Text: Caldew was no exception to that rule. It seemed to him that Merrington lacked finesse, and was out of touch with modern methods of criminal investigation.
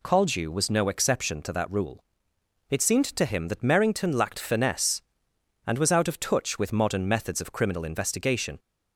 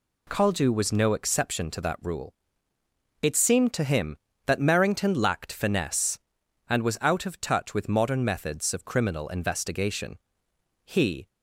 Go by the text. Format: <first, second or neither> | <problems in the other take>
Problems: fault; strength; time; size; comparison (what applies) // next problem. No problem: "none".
first | goes on to say "He"; slight; from 10.8 s on; 0.44 s long